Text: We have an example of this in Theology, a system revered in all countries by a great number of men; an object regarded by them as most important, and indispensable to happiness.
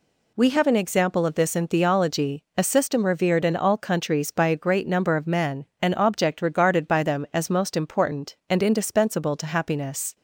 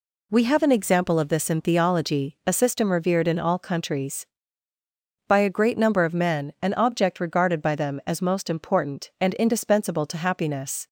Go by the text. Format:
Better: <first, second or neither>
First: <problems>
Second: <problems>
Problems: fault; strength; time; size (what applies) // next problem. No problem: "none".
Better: neither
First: none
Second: none